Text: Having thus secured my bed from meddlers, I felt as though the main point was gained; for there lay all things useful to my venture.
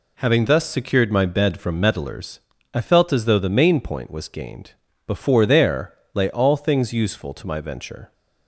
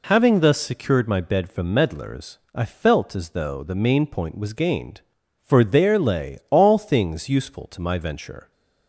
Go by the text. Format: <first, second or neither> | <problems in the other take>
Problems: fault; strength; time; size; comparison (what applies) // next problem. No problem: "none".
second | says "before" for "for"; at 5.0 s // pauses between "there" and "lay"; slight; at 5.9 s; 0.18 s long